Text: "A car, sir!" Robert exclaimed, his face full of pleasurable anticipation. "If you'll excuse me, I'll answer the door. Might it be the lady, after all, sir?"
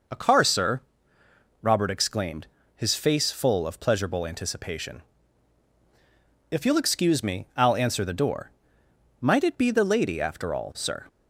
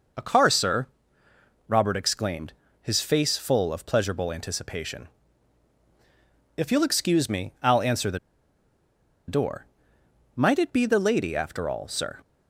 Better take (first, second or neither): first